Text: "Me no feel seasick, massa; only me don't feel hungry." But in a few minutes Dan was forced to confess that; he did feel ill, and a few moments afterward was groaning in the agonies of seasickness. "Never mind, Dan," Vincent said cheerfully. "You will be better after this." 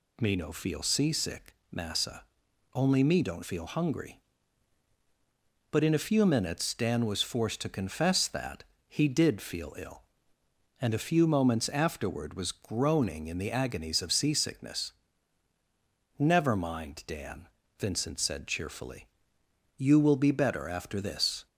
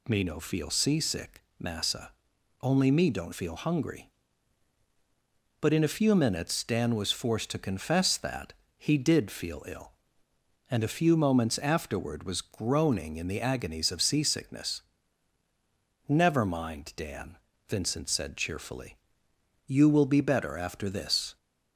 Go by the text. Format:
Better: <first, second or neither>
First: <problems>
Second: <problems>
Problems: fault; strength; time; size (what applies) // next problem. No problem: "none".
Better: neither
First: none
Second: none